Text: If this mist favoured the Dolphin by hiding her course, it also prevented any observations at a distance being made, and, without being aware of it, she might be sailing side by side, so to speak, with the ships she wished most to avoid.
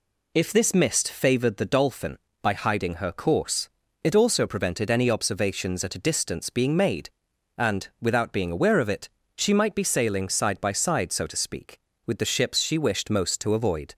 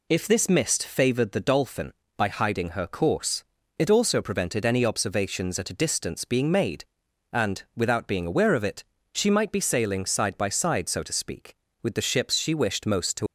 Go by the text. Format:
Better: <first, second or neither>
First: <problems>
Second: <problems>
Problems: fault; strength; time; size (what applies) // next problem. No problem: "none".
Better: first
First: none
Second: stops before "avoid"; at 13.2 s